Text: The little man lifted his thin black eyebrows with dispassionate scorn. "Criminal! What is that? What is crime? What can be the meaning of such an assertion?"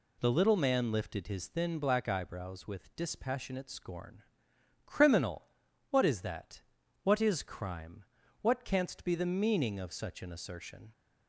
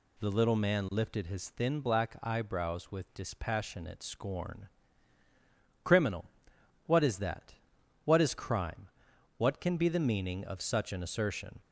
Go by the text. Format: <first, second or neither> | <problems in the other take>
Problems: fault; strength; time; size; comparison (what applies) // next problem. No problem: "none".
second | says "canst" for "can"; at 8.6 s